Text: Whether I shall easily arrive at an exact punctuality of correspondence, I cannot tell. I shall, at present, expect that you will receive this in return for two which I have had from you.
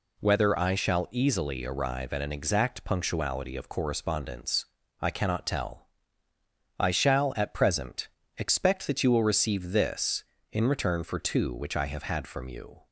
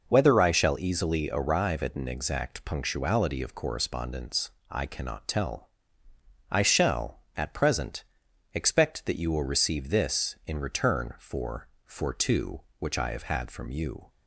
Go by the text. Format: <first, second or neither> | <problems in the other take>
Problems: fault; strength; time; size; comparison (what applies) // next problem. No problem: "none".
first | says "for" twice; at 11.8 s